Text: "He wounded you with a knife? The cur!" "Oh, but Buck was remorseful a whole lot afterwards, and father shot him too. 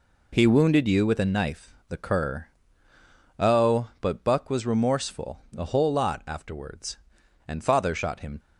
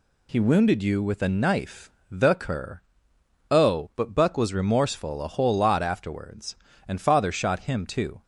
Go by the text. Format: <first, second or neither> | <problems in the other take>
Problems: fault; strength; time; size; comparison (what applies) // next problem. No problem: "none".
second | stops before "too"; at 8.3 s